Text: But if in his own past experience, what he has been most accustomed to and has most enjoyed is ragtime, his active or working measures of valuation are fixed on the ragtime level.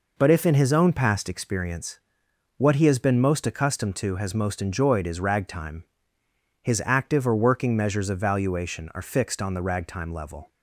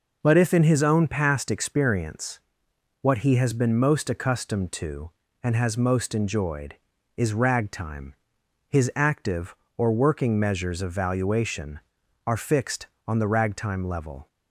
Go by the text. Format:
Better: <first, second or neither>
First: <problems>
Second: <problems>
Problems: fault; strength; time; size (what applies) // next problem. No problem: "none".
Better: second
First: skips "and"; at 4.1 s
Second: none